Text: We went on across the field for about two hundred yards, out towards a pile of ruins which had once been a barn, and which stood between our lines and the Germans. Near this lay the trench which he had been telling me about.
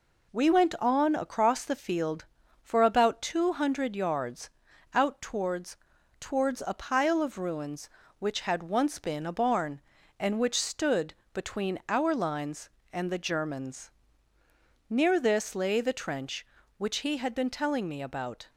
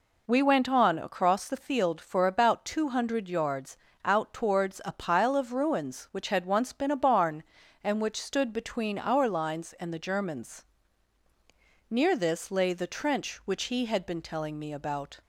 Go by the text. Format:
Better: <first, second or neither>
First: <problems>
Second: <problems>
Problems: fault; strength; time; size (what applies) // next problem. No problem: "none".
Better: second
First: says "towards" twice; at 6.1 s // pauses between "stood" and "between"; slight; at 11.1 s; 0.18 s long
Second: none